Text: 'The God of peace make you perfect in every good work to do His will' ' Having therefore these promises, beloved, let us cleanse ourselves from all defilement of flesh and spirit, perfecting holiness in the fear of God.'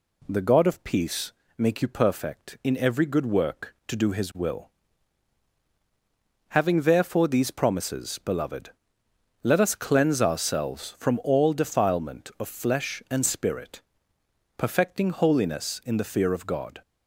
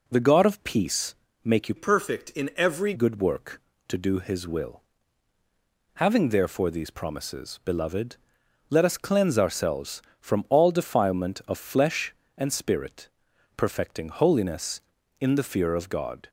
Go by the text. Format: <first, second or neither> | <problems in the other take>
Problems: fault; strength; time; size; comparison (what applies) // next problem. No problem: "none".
first | pauses between "peace" and "make"; slight; at 1.1 s; 0.26 s long; slight in the first // changes voice from "perfect" to "every"; from 1.7 to 2.9 s; 1.2 s long